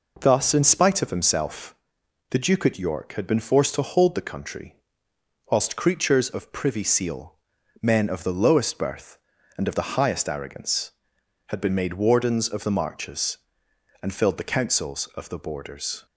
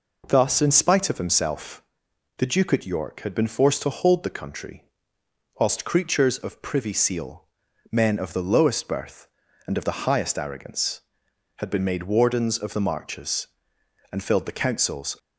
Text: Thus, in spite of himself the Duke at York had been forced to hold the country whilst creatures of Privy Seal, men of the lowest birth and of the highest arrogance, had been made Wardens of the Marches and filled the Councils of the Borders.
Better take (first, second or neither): first